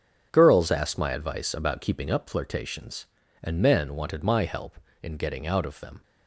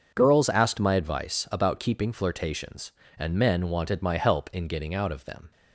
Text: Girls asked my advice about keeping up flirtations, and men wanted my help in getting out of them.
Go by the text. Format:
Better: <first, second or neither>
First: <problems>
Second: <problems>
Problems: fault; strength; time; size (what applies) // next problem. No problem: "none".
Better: first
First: starts louder than the rest; strong; until 1.3 s; 7 dB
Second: starts louder than the rest; until 1.1 s; 6.5 dB // skips "up"; at 2.1 s